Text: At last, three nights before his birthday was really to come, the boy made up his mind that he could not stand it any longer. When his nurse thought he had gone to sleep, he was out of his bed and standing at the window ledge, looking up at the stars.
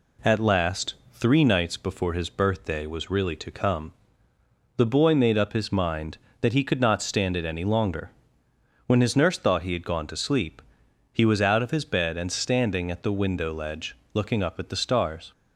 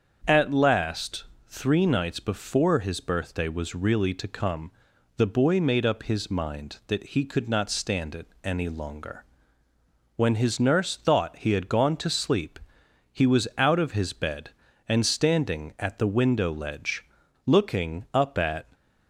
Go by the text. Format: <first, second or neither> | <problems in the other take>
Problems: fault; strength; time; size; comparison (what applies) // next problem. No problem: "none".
first | starts louder than the rest; strong; until 1.5 s; 7.5 dB // pauses between "it" and "any"; slight; at 8.2 s; 0.16 s long // stops before "the stars"; at 18.7 s